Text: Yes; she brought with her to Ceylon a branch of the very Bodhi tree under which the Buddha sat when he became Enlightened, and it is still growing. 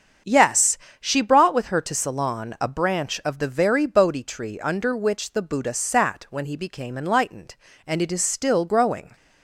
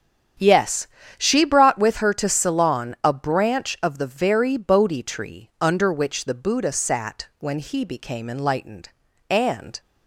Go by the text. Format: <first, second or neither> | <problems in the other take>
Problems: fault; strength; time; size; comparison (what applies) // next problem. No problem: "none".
first | starts louder than the rest; strong; until 1.7 s; 8.5 dB; strong in the first // stops before "it is still growing"; at 9.7 s